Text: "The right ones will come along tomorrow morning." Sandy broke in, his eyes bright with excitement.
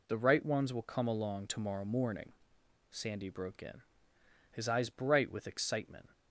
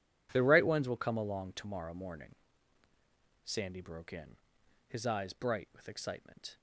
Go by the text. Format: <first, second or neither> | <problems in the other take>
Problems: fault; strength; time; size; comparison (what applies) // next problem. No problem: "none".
neither | none